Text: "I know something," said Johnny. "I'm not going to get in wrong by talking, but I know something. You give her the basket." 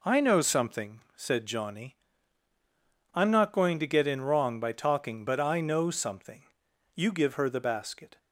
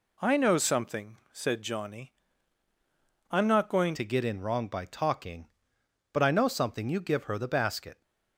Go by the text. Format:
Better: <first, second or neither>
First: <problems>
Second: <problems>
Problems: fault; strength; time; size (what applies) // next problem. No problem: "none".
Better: first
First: none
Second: changes voice at "to"; from 3.9 s on; 4.1 s long